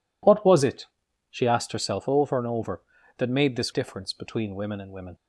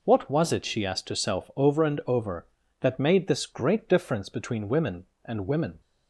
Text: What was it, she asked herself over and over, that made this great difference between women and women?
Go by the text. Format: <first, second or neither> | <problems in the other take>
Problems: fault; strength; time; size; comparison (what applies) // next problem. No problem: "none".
second | skips "great"; at 3.7 s